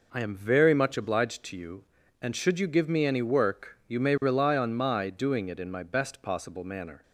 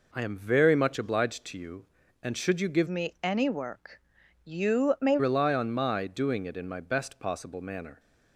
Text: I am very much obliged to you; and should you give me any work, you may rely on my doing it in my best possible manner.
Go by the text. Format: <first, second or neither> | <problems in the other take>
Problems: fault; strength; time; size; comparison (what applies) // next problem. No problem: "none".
first | changes voice from "me" to "may"; from 2.8 to 5.1 s; 2.3 s long